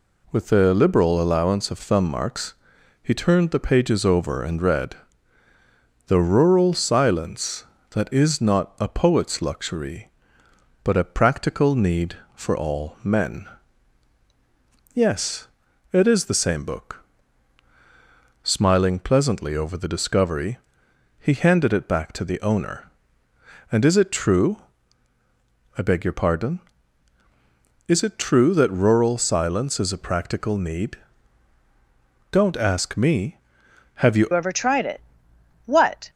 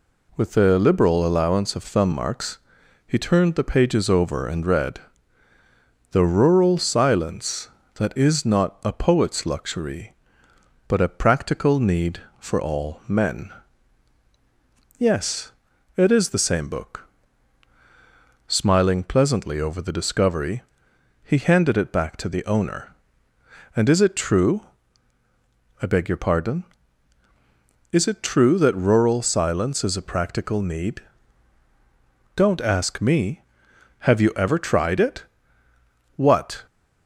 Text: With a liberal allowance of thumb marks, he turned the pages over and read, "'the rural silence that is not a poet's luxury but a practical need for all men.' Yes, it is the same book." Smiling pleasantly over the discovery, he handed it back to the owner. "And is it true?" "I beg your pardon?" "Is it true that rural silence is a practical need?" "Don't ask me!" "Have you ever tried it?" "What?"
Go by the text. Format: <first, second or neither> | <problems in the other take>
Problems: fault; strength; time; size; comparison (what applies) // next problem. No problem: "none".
second | changes voice at "ever"; from 34.3 s on; 1.7 s long